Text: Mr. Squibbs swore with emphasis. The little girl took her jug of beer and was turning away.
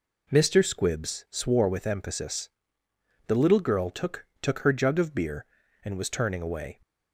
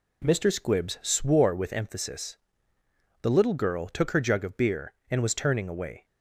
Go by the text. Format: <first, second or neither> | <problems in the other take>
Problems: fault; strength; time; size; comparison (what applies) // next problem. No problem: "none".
second | says "took" twice; at 4.4 s